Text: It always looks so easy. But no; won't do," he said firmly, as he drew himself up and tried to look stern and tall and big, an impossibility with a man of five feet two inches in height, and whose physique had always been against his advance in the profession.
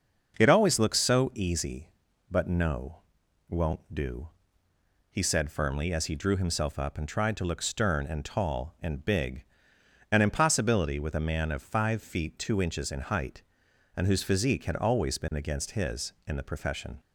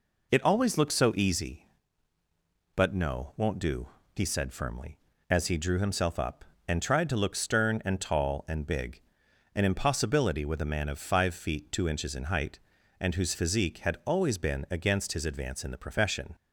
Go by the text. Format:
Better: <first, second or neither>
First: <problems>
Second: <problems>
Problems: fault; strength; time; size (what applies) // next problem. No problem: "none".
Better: second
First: starts louder than the rest; until 1.3 s; 6 dB // skips "advance"; at 16.1 s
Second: none